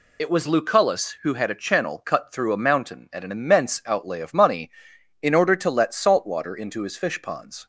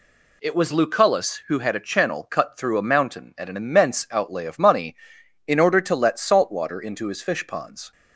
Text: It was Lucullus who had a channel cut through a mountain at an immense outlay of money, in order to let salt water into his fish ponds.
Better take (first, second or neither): second